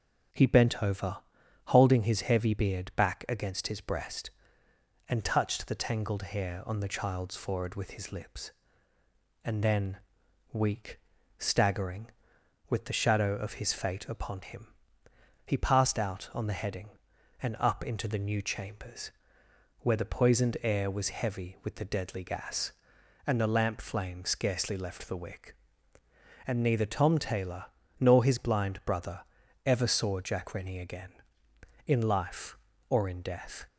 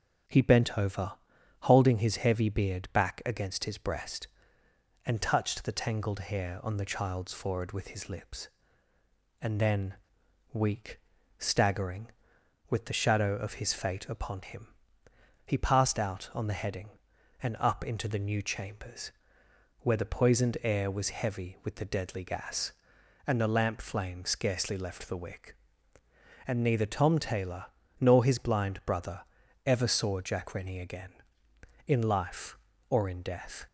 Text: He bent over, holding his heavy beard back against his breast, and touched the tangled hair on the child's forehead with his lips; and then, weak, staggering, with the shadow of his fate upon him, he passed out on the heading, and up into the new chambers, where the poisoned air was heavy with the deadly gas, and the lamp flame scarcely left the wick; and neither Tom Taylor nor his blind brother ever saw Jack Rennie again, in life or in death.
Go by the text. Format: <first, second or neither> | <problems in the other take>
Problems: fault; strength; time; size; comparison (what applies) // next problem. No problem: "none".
neither | starts louder than the rest; strong; the same in both // pauses between "Taylor" and "nor"; slight; the same in both // pauses between "brother" and "ever"; the same in both